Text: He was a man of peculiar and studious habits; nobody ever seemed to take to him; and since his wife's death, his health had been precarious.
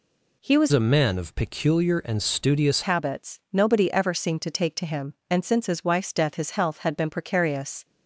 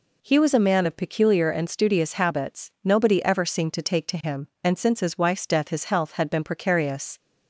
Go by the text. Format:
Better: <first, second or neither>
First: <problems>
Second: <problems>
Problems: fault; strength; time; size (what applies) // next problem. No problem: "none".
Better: second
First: changes voice from "a" to "studious"; from 0.7 to 2.8 s; 2.1 s long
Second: none